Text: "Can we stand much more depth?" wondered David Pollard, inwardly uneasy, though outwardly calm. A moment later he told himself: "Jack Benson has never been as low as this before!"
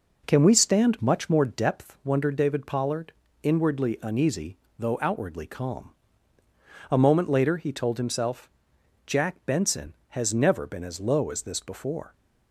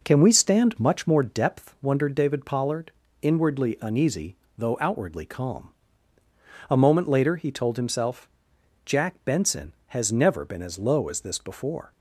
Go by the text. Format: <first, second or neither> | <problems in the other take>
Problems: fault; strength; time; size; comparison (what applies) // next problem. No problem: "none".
neither | none